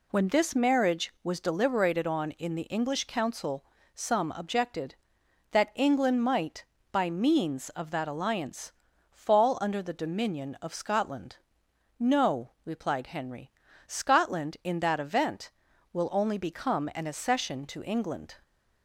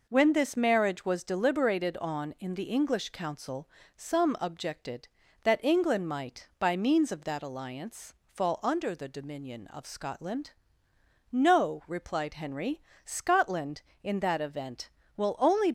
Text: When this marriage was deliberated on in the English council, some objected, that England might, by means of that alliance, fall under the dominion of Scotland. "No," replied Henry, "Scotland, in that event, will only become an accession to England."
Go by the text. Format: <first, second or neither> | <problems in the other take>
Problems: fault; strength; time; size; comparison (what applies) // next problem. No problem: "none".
first | stops before "become an accession to England"; at 15.6 s